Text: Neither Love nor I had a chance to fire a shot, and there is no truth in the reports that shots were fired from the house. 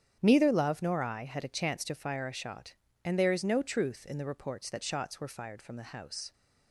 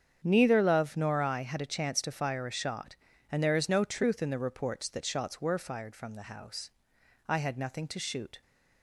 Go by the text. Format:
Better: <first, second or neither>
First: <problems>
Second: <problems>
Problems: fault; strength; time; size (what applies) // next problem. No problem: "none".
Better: first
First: starts louder than the rest; strong; until 1.2 s; 8.5 dB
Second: starts louder than the rest; strong; until 1.2 s; 8 dB // goes on to say "I had nothing to shoot"; noticeable; from 7.2 s on; 1.1 s long